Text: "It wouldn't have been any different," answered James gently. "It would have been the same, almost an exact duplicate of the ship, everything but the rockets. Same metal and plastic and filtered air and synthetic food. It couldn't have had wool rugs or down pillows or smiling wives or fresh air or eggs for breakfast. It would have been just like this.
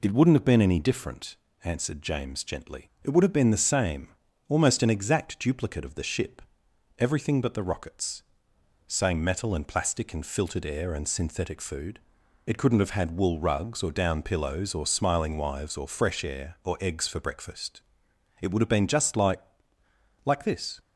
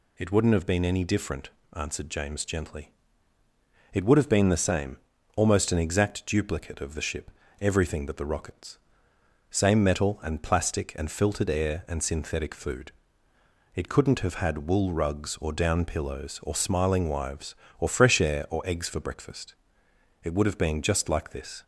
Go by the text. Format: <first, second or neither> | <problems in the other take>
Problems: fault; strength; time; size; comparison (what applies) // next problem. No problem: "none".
second | says "like" twice; at 20.2 s